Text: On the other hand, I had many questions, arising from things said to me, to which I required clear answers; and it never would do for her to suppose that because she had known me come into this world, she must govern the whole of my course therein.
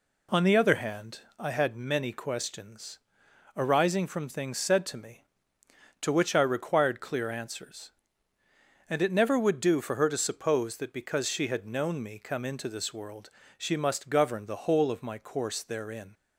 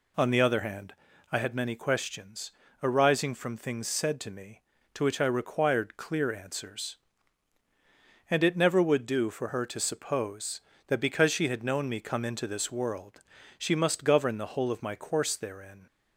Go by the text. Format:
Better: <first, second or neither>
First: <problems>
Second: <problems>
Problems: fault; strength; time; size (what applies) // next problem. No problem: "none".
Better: neither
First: none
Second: none